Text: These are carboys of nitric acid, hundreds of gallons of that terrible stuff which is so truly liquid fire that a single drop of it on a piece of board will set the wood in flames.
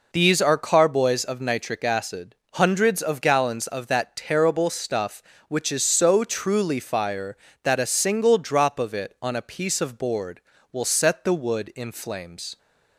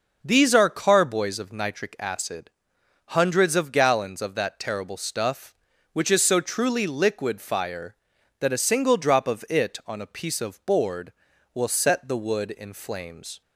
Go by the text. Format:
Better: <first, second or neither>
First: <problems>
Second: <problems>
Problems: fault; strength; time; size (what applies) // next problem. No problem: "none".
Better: second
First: skips "liquid"; at 6.7 s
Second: none